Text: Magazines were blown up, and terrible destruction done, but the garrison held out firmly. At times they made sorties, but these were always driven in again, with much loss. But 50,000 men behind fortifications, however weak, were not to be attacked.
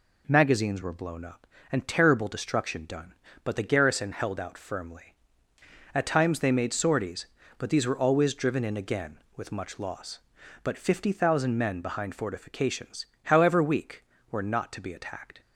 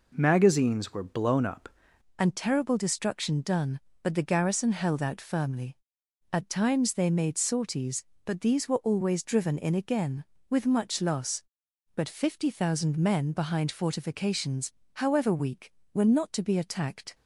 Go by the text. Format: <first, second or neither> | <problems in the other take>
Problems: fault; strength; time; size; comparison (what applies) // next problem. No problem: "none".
first | changes voice at "and"; from 2.1 s on; 15.0 s long